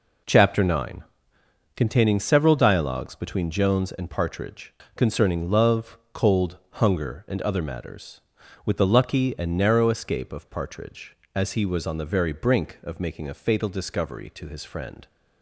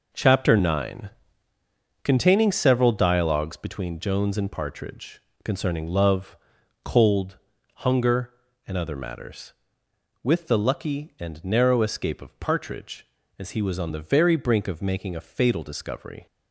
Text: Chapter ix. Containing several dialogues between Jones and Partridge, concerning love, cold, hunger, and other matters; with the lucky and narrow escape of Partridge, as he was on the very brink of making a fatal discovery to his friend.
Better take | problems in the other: first | stops before "to his friend"; at 16.2 s

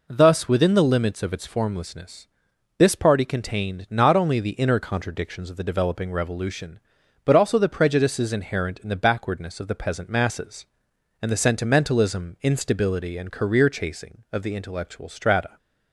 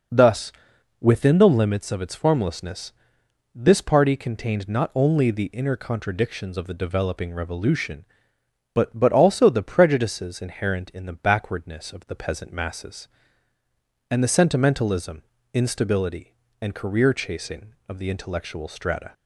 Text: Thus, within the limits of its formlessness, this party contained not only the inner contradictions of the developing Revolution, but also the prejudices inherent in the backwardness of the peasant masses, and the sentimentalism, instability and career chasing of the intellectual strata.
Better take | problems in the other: first | says "but" twice; at 8.9 s

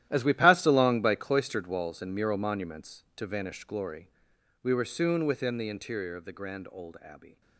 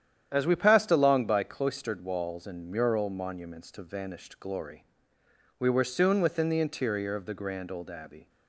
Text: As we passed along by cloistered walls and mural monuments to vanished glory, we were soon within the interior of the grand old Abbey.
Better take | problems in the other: second | gets quieter; strong; throughout; 15 dB // starts louder than the rest; strong; until 1.1 s; 12.5 dB; strong in the second

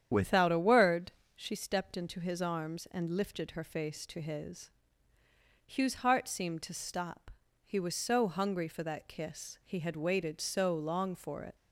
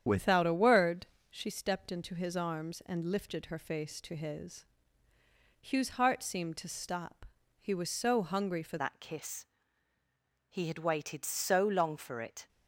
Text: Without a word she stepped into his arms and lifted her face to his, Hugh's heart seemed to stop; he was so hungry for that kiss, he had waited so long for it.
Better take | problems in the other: first | starts louder than the rest; strong; until 1.3 s; 9 dB; strong in the first // pauses between "word" and "she"; slight; at 1.0 s; 0.24 s long; slight in the first // changes voice at "that"; from 8.7 s on; 3.7 s long

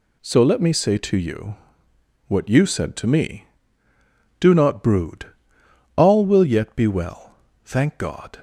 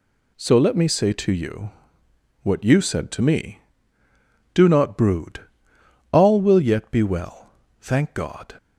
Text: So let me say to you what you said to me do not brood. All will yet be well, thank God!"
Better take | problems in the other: neither | pauses between "you" and "what"; noticeable; the same in both

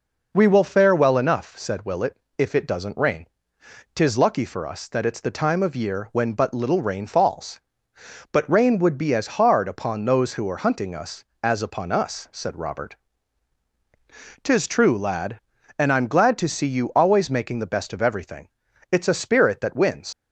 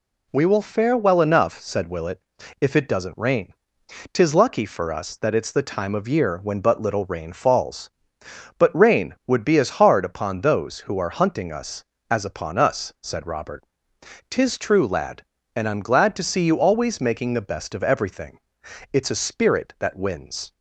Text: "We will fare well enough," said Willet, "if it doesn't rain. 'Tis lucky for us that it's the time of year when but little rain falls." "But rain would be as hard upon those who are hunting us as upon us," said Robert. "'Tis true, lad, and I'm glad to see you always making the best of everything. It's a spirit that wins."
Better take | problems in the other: second | leaves "wins" unfinished; at 20.1 s; 100 ms

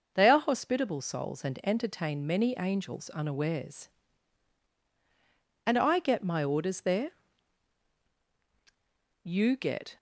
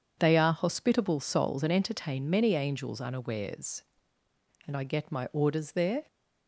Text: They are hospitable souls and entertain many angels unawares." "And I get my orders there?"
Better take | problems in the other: second | goes on to say "You get"; noticeable; from 9.2 s on; 0.74 s long

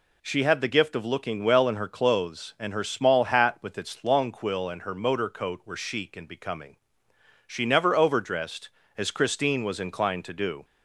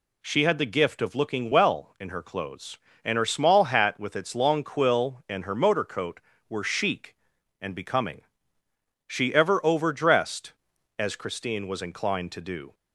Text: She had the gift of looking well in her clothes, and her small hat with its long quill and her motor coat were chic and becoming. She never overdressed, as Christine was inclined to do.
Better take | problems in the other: first | says "ever" for "never"; at 9.3 s

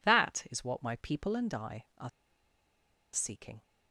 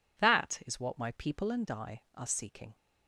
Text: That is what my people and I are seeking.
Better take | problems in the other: second | pauses between "are" and "seeking"; at 2.0 s; 1.0 s long

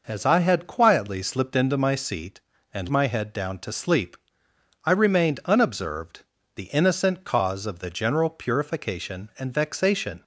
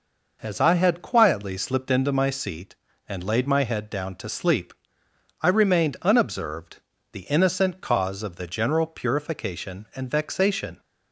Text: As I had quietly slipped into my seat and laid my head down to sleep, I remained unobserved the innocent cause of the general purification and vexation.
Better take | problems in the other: second | skips "laid"; at 2.9 s // pauses between "unobserved" and "the"; slight; at 6.2 s; 0.32 s long; slight in the second

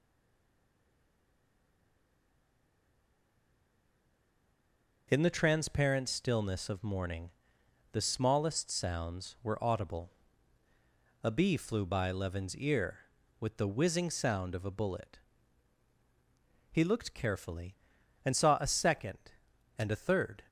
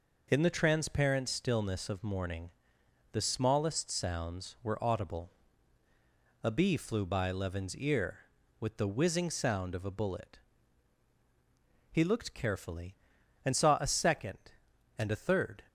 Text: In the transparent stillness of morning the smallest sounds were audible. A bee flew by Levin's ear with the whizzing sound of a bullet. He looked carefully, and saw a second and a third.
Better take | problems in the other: second | stays silent before the first word; strong; until 5.0 s; 5.0 s long // pauses between "morning" and "the"; noticeable; at 7.3 s; 0.62 s long; noticeable in the second

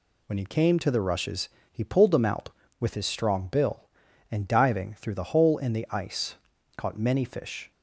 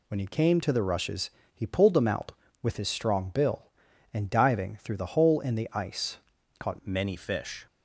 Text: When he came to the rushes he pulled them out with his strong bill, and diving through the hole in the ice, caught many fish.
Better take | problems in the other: first | pauses between "rushes" and "he"; slight; at 1.2 s; 0.24 s long; slight in the first // changes voice at "many"; from 6.8 s on; 0.8 s long

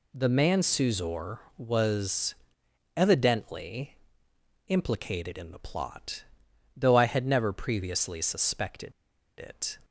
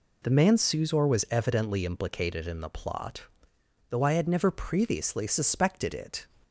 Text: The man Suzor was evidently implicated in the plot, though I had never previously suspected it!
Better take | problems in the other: second | pauses between "was" and "evidently"; noticeable; at 2.3 s; 0.64 s long // pauses between "evidently" and "implicated"; noticeable; at 3.9 s; 0.70 s long // pauses between "suspected" and "it"; noticeable; at 8.9 s; 0.48 s long

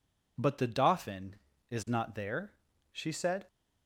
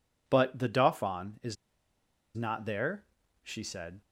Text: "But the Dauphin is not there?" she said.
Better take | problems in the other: first | pauses between "is" and "not"; noticeable; at 1.5 s; 0.79 s long

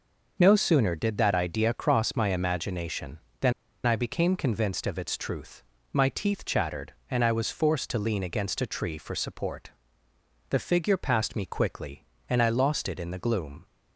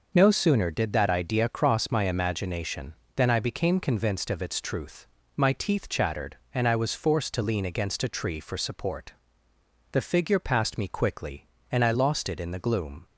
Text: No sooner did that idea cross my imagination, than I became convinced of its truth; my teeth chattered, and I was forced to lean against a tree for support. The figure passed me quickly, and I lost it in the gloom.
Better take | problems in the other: second | pauses between "than" and "I"; slight; at 3.5 s; 0.33 s long

